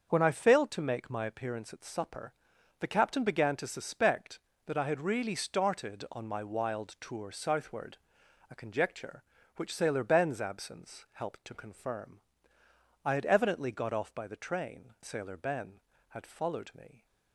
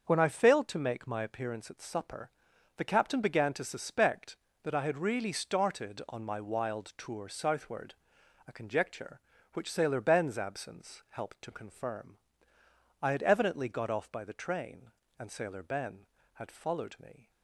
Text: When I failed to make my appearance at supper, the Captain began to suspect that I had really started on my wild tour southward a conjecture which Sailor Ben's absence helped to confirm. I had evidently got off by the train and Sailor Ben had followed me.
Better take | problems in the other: second | starts louder than the rest; until 1.1 s; 6.5 dB; also in the second // pauses between "southward" and "a"; noticeable; at 7.9 s; 0.52 s long; noticeable in the second // skips "and"; at 14.9 s

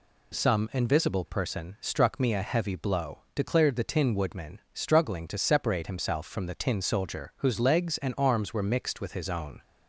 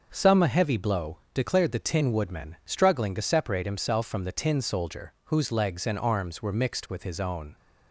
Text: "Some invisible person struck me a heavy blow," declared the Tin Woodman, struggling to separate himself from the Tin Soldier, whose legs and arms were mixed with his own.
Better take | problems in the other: first | skips "invisible person struck me"; at 0.4 s

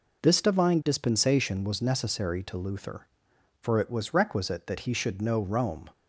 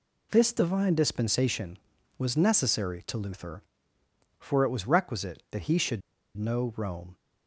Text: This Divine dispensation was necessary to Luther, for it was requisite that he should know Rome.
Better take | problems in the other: first | pauses between "should" and "know"; slight; at 6.0 s; 0.36 s long

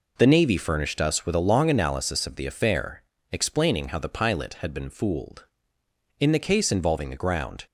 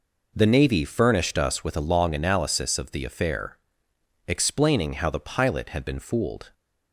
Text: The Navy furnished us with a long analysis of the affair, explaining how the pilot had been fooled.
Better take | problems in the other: second | goes on to say "In the case involving the ground"; from 6.2 s on; 1.4 s long

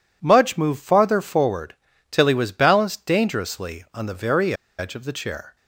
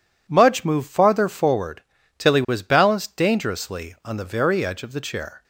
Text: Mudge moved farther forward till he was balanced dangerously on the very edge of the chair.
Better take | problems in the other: second | pauses between "forward" and "till"; slight; at 1.7 s; 0.36 s long; slight in the second // pauses between "very" and "edge"; slight; at 4.5 s; 0.26 s long

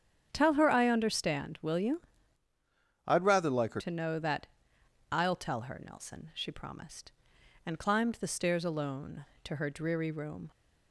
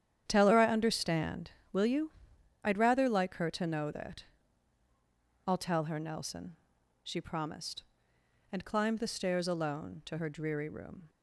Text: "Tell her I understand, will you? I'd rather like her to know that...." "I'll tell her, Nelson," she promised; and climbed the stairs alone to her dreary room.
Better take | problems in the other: second | starts louder than the rest; strong; until 1.3 s; 8.5 dB; strong in the second // changes voice from "I'd" to "her"; from 3.0 to 3.8 s; 0.8 s long

